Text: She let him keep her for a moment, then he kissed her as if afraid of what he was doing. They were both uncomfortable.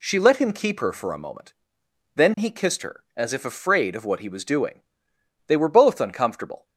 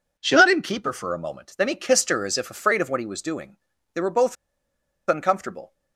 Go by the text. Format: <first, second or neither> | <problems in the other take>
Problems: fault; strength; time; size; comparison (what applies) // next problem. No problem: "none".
first | pauses between "both" and "uncomfortable"; noticeable; at 4.3 s; 0.72 s long